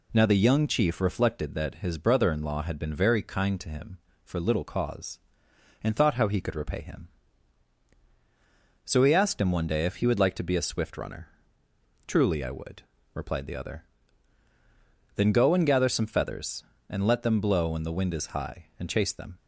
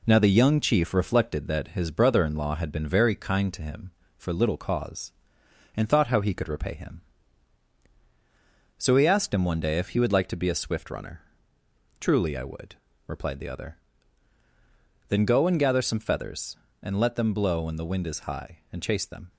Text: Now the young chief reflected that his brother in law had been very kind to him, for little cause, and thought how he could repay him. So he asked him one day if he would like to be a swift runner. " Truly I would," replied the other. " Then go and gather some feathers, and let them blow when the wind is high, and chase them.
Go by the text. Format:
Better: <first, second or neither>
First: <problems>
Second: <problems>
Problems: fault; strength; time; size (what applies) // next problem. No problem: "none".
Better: first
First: none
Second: gets quieter; strong; throughout; 8.5 dB